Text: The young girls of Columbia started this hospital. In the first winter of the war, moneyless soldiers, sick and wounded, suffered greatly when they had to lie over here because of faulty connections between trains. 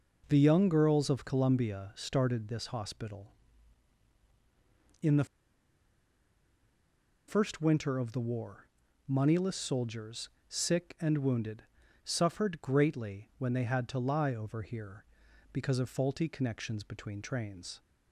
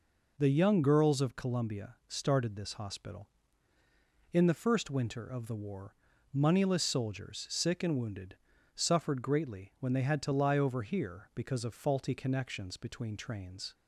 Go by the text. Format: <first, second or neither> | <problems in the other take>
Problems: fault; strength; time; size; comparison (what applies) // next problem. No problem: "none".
second | pauses between "the" and "first"; strong; at 5.2 s; 2.0 s long